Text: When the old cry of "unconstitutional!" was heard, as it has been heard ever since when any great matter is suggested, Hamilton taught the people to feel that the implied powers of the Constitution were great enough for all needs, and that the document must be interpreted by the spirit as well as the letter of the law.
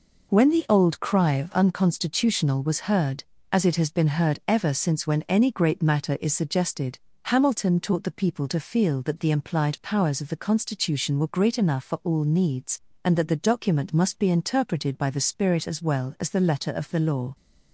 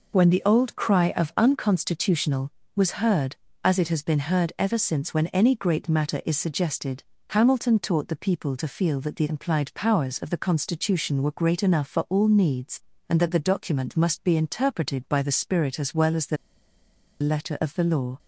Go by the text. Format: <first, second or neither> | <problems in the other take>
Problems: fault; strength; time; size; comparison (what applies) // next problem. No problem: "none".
first | pauses between "the" and "letter"; noticeable; at 16.3 s; 0.85 s long